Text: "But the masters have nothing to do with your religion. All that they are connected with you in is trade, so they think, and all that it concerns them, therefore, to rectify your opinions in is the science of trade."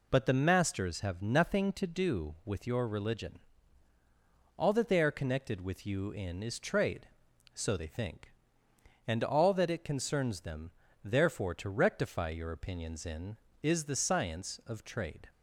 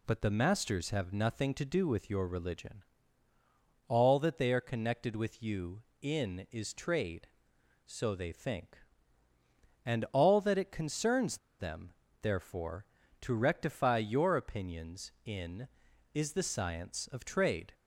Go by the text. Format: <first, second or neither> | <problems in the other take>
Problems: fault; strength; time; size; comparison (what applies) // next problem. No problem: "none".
first | pauses between "concerns" and "them"; slight; at 11.3 s; 0.21 s long